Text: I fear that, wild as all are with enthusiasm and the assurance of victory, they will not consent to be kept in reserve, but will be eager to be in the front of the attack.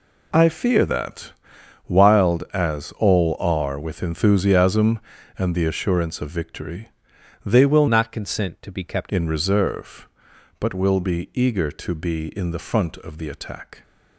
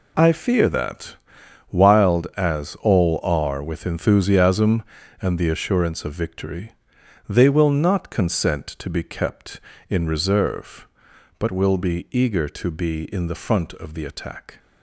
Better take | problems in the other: second | changes voice from "not" to "kept"; from 7.8 to 9.1 s; 1.3 s long

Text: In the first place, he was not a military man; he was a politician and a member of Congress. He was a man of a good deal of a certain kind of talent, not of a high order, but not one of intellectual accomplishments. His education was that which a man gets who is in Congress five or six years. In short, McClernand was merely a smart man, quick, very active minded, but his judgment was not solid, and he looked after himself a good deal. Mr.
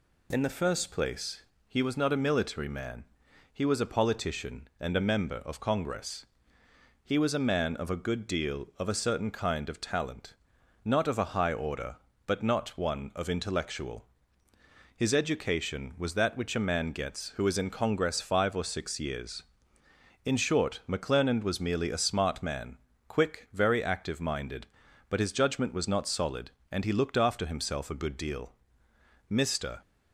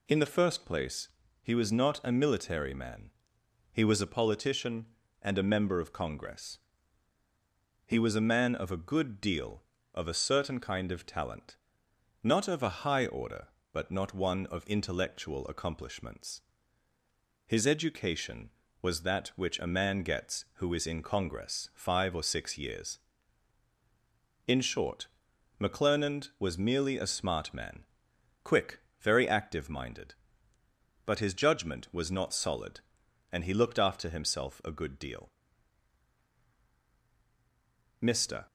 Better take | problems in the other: second | skips "accomplishments"; at 14.5 s

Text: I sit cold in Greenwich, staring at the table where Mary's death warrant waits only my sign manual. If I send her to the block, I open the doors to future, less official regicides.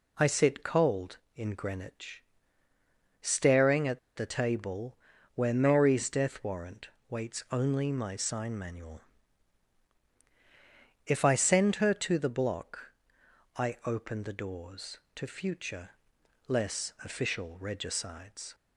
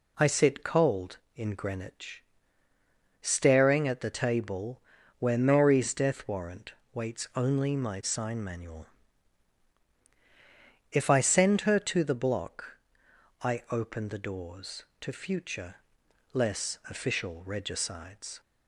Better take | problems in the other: second | pauses between "at" and "the"; slight; at 3.9 s; 0.17 s long // pauses between "table" and "where"; at 4.9 s; 0.38 s long; also in the second // pauses between "warrant" and "waits"; slight; at 6.8 s; 0.22 s long; slight in the second

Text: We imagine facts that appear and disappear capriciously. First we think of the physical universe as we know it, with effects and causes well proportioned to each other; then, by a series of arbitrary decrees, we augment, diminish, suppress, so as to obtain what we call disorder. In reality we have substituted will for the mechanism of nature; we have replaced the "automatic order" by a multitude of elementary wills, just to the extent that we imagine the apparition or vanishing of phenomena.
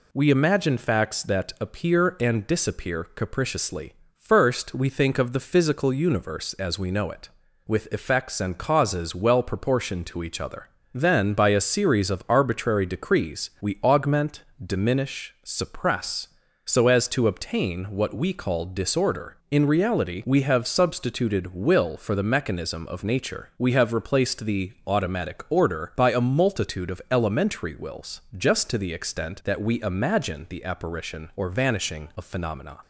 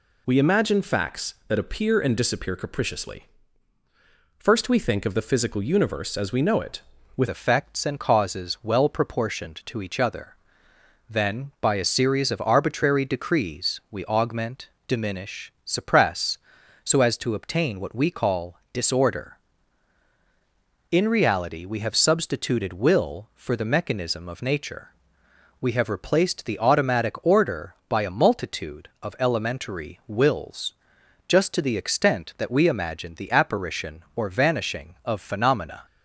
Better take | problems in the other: first | changes voice at "effects"; from 7.2 s on; 28.6 s long // pauses between "call" and "disorder"; slight; at 18.5 s; 0.16 s long

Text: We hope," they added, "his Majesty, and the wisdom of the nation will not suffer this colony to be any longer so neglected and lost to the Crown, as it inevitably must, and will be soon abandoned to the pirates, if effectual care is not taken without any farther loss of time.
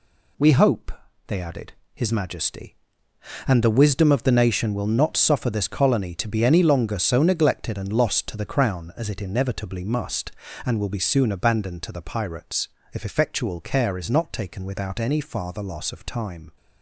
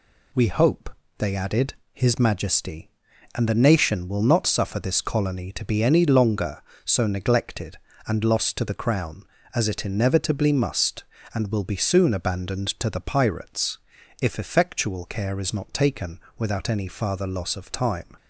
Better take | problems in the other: first | skips "the wisdom of"; at 3.4 s // pauses between "taken" and "without"; slight; at 16.2 s; 0.18 s long

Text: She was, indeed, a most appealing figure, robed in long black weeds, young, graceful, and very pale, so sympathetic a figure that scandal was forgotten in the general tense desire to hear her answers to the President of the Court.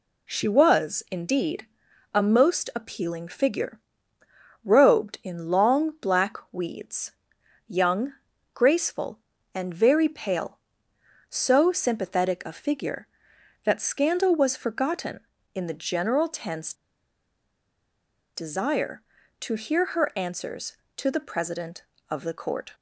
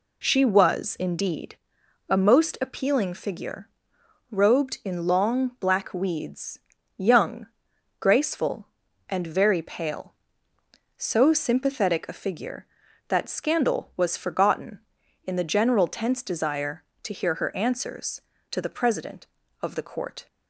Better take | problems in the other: second | pauses between "tense" and "desire"; strong; at 16.7 s; 1.6 s long

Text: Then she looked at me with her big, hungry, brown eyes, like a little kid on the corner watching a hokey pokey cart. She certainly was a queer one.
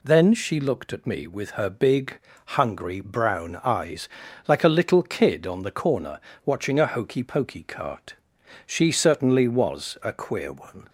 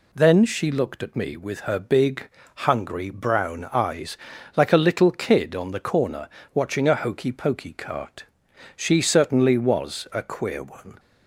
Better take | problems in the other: neither | pauses between "corner" and "watching"; slight; the same in both

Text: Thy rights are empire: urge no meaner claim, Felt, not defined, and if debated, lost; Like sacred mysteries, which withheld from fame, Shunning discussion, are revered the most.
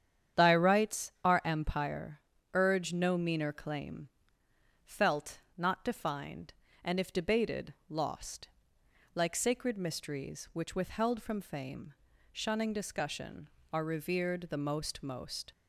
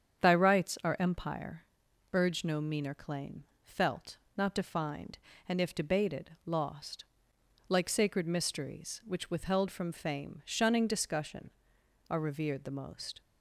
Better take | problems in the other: second | starts louder than the rest; strong; until 1.5 s; 9 dB; strong in the second // says "most" twice; at 15.0 s

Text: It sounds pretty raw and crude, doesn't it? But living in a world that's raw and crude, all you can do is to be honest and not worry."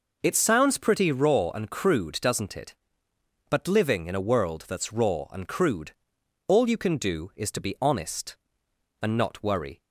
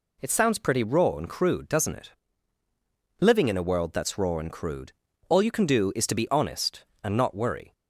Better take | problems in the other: first | skips "But"; at 2.6 s

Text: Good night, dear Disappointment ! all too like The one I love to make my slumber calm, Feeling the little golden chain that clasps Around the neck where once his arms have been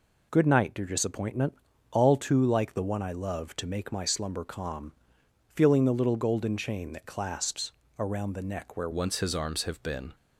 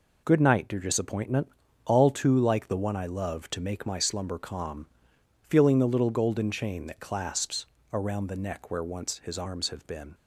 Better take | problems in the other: second | pauses between "clasps" and "Around"; slight; at 7.7 s; 0.26 s long; slight in the second // changes voice at "once"; from 8.9 s on; 1.2 s long

